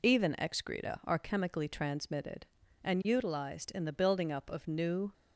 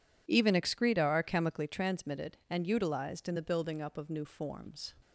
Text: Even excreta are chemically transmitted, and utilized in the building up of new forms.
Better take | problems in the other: second | stops before "forms"; at 5.1 s

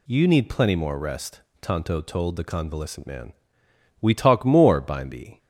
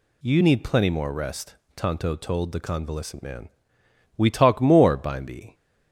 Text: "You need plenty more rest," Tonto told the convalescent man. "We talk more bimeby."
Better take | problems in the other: neither | none

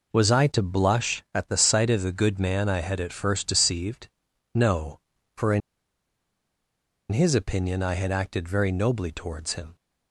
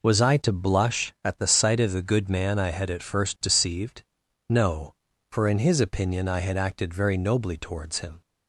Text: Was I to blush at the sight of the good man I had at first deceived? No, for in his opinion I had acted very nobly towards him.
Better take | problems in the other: second | pauses between "in" and "his"; strong; at 5.6 s; 1.5 s long

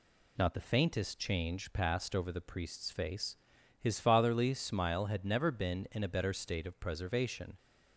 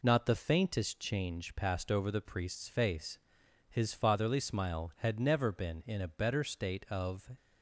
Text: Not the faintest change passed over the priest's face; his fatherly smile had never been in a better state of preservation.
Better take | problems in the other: first | stops before "preservation"; at 7.3 s

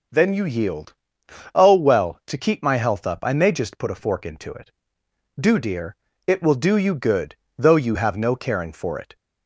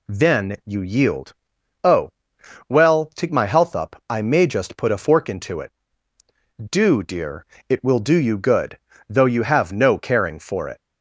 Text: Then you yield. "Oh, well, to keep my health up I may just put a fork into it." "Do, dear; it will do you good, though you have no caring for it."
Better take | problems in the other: first | skips "keep"; at 3.2 s

